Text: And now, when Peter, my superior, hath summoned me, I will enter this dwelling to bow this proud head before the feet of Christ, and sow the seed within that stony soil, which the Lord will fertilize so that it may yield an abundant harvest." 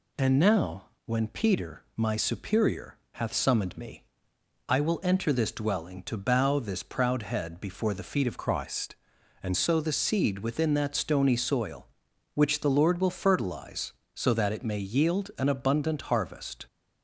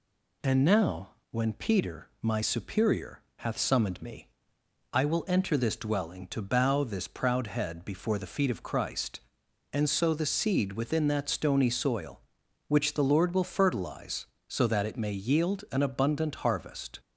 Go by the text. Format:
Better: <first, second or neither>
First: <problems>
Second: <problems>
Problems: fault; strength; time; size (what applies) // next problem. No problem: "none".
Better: second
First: changes voice from "Christ" to "and"; from 8.3 to 9.5 s; 1.2 s long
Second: none